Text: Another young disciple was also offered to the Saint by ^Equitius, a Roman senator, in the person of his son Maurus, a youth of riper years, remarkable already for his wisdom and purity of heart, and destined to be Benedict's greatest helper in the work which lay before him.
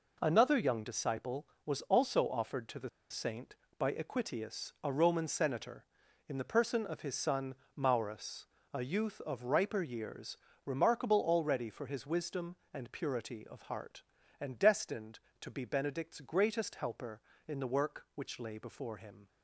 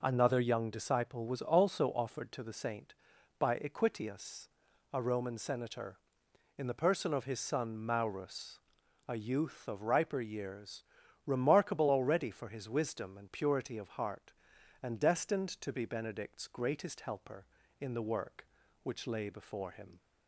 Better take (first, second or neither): second